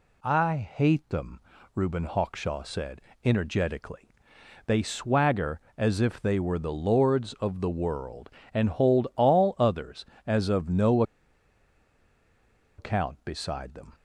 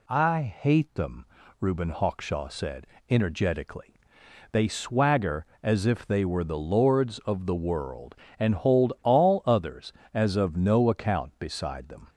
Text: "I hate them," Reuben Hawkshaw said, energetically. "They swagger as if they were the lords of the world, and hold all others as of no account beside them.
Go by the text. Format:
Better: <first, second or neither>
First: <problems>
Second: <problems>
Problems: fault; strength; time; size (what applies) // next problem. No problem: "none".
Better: second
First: pauses between "no" and "account"; strong; at 11.0 s; 1.7 s long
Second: none